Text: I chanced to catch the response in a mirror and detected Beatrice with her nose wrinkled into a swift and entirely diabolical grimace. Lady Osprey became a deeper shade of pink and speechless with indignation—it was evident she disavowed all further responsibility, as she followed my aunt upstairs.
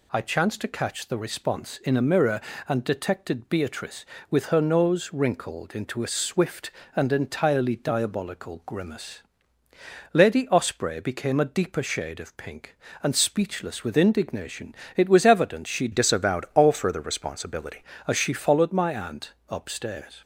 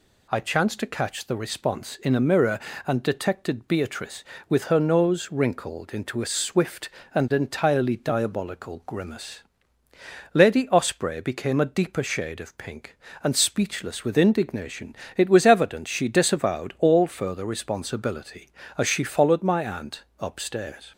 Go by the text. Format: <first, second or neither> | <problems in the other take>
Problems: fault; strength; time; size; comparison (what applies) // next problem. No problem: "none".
second | changes voice from "disavowed" to "responsibility"; from 15.9 to 17.8 s; 1.9 s long // pauses between "aunt" and "upstairs"; slight; at 19.3 s; 0.16 s long; slight in the second